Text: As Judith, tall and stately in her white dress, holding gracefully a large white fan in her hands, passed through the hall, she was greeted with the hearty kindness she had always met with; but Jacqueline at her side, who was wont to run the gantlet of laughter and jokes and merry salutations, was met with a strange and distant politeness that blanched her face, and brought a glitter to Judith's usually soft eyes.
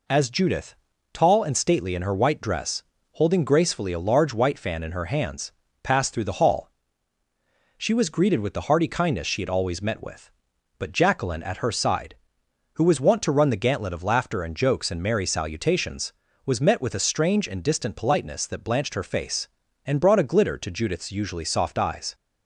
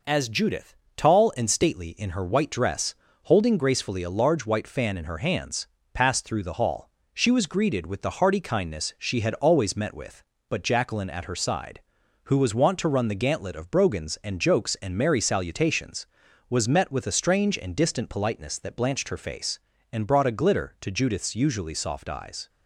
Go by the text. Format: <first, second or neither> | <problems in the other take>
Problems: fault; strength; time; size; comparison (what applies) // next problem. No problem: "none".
first | says "brogans" for "laughter"; at 13.7 s